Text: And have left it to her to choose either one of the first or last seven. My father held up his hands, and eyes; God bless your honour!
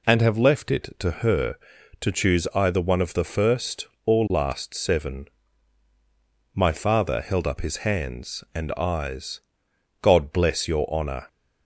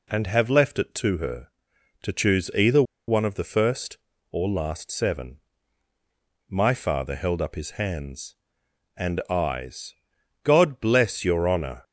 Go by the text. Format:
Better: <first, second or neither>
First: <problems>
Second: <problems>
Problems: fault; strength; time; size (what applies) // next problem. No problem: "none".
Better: first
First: none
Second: pauses between "either" and "one"; slight; at 2.8 s; 0.25 s long